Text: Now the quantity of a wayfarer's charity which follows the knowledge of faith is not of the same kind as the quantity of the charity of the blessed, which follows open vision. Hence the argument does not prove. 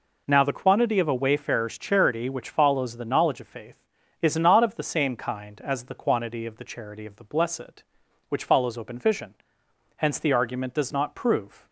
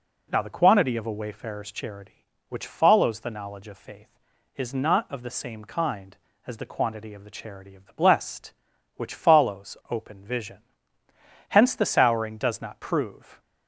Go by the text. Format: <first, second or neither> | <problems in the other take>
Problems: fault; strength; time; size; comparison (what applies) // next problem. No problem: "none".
first | says "souring" for "argument"; at 11.8 s